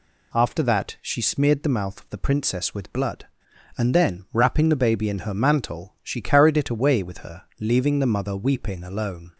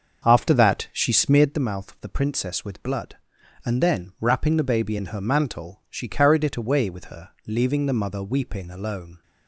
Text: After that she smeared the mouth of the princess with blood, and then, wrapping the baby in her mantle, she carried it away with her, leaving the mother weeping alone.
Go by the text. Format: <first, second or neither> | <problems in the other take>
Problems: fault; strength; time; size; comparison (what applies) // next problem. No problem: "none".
first | starts louder than the rest; until 1.6 s; 6.5 dB